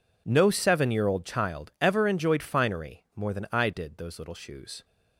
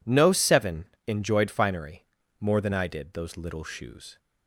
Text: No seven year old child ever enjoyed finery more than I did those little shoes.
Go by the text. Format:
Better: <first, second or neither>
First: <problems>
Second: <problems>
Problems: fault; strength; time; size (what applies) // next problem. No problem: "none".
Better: first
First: none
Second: skips "year old child ever"; at 0.9 s // pauses between "finery" and "more"; at 2.0 s; 0.38 s long